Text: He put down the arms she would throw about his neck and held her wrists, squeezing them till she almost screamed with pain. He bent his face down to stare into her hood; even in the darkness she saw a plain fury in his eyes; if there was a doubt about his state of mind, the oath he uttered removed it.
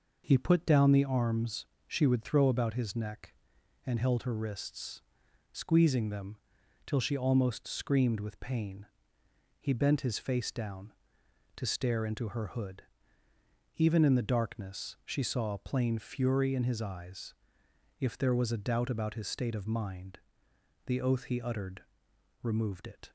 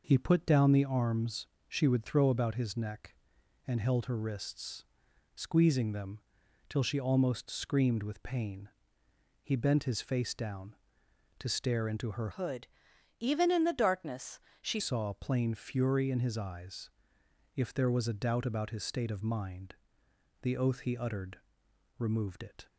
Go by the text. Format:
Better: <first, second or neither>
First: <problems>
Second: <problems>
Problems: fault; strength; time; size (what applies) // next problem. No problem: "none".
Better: first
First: pauses between "arms" and "she"; slight; at 1.6 s; 0.20 s long // pauses between "them" and "till"; noticeable; at 6.3 s; 0.50 s long // pauses between "uttered" and "removed"; noticeable; at 21.8 s; 0.60 s long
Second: pauses between "arms" and "she"; slight; at 1.4 s; 0.20 s long // pauses between "them" and "till"; noticeable; at 6.1 s; 0.50 s long // changes voice from "hood" to "she"; from 12.3 to 14.7 s; 2.4 s long // pauses between "darkness" and "she"; slight; at 14.3 s; 0.22 s long // pauses between "uttered" and "removed"; noticeable; at 21.3 s; 0.60 s long